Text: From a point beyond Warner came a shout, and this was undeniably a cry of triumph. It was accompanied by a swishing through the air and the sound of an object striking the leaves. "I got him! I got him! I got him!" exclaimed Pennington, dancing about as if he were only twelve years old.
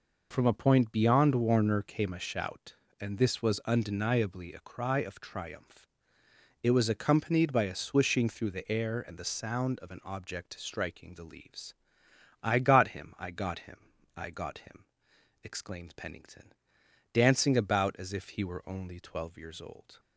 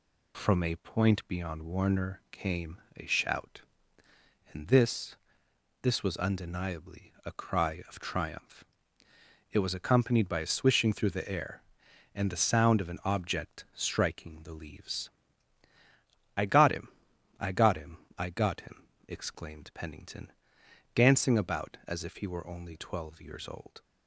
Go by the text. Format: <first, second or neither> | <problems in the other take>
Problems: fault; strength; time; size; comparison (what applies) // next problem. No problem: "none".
first | pauses between "came" and "a"; slight; at 2.7 s; 0.16 s long // says "this" twice; at 5.8 s